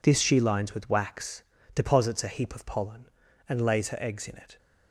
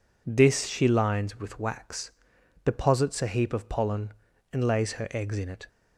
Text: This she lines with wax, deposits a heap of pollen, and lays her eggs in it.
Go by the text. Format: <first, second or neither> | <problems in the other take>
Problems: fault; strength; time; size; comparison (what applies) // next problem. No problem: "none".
neither | none